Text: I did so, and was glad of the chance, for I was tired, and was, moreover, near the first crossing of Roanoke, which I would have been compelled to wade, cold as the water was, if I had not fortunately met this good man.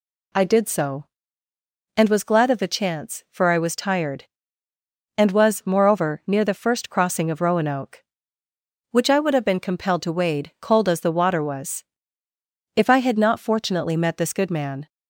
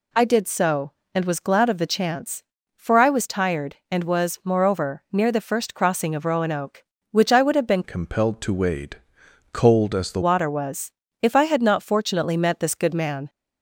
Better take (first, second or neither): first